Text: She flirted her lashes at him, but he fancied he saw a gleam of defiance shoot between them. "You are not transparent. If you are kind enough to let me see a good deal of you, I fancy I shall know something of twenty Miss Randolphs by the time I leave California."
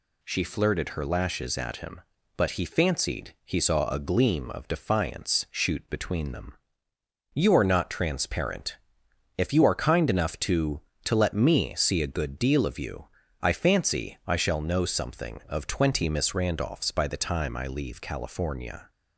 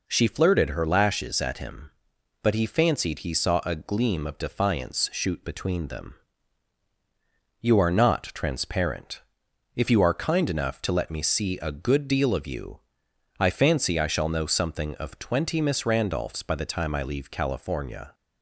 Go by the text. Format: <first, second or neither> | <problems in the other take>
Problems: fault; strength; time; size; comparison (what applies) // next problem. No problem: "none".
second | says "to" twice; at 11.0 s